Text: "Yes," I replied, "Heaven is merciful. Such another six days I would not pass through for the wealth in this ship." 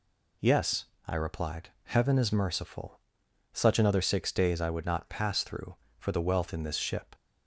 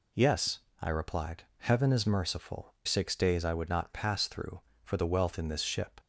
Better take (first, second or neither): first